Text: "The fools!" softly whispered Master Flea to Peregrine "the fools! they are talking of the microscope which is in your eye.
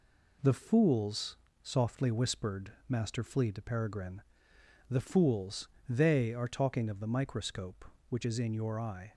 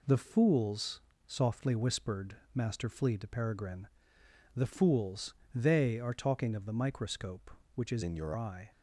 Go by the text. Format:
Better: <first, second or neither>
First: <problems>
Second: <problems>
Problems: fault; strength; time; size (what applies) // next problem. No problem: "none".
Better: first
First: pauses between "whispered" and "Master"; slight; at 2.7 s; 0.16 s long // pauses between "Peregrine" and "the"; noticeable; at 4.2 s; 0.66 s long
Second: pauses between "whispered" and "Master"; slight; at 2.3 s; 0.18 s long // pauses between "Peregrine" and "the"; noticeable; at 3.8 s; 0.66 s long // changes voice from "in" to "your"; from 8.0 to 8.3 s; 0.3 s long